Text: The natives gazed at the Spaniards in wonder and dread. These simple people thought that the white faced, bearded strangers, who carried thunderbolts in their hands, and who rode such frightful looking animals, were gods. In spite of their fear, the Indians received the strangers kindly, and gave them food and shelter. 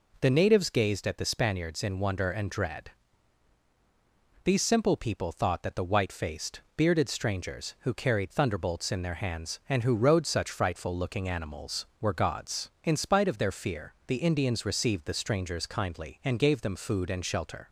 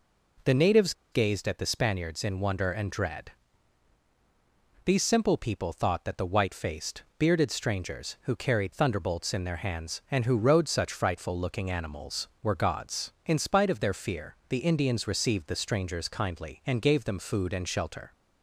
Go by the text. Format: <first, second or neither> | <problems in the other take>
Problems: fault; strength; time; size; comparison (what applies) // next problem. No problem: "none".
first | pauses between "natives" and "gazed"; slight; at 0.9 s; 0.19 s long